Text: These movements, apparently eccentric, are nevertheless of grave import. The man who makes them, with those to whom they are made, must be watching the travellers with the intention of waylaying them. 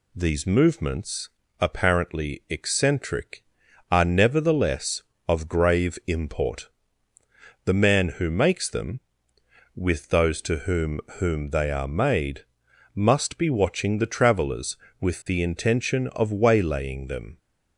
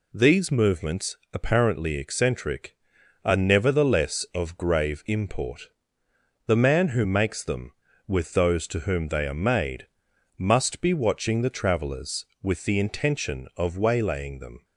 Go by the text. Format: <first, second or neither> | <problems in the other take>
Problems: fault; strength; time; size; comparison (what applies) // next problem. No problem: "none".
second | says "whom" twice; at 11.1 s